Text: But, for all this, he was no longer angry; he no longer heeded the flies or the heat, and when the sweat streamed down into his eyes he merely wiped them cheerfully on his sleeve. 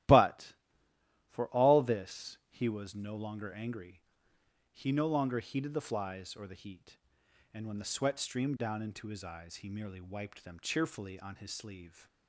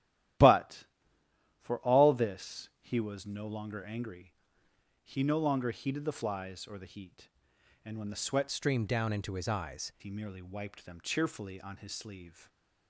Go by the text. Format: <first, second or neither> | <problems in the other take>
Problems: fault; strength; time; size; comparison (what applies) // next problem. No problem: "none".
first | starts louder than the rest; strong; until 2.1 s; 13 dB; strong in the first // changes voice from "streamed" to "eyes"; from 8.5 to 9.9 s; 1.4 s long // stays silent after the last word; slight; from 12.3 s on; 0.5 s long